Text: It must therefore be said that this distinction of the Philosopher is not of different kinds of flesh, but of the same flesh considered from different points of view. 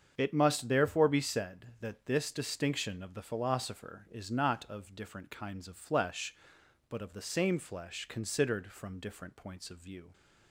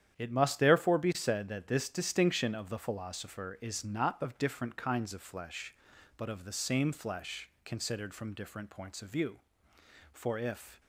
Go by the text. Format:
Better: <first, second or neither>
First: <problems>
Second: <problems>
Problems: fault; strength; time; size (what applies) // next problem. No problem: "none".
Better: first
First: starts louder than the rest; strong; until 1.2 s; 7.5 dB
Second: starts louder than the rest; strong; until 1.1 s; 9.5 dB // goes on to say "For if"; noticeable; from 10.1 s on; 0.68 s long